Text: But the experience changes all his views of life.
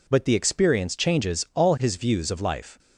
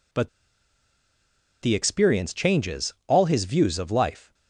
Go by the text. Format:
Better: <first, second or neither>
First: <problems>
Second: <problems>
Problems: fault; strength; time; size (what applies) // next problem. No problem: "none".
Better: first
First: none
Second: pauses between "But" and "the"; strong; at 0.2 s; 1.3 s long